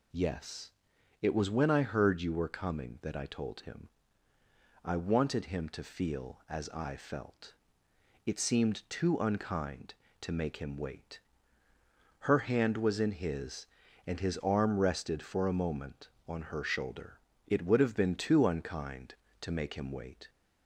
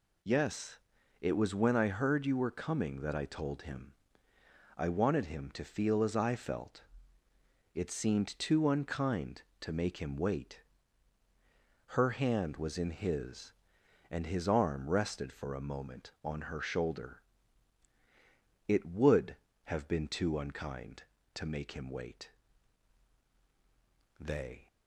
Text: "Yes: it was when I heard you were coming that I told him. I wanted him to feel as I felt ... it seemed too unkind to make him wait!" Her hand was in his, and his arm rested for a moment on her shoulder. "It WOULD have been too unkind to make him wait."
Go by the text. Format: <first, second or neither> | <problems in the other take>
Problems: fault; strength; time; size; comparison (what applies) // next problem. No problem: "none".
first | goes on to say "They"; slight; from 24.1 s on; 0.48 s long